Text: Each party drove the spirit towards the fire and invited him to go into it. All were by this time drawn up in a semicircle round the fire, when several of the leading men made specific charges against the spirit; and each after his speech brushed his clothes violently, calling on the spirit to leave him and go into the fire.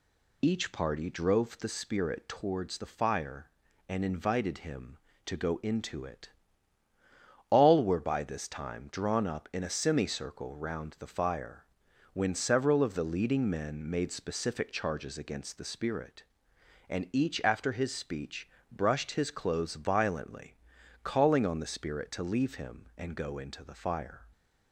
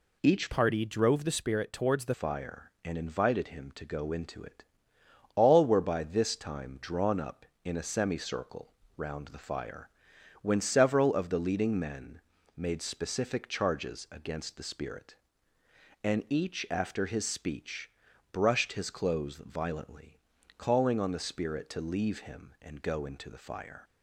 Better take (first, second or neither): first